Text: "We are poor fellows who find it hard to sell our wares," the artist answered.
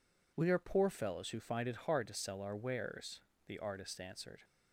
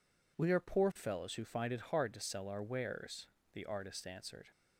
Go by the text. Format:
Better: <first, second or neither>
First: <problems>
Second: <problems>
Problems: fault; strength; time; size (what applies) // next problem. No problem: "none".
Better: neither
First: none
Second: none